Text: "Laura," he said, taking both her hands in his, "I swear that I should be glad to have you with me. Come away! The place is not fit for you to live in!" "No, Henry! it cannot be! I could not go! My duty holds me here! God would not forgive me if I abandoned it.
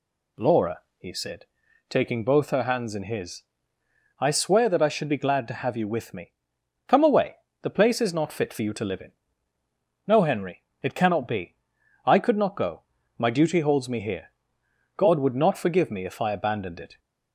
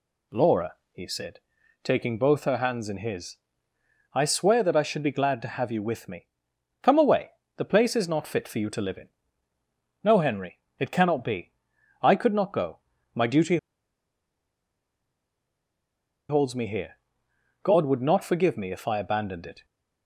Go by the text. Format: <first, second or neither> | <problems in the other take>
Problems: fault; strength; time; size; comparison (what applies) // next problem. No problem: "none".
first | pauses between "duty" and "holds"; strong; at 13.5 s; 2.7 s long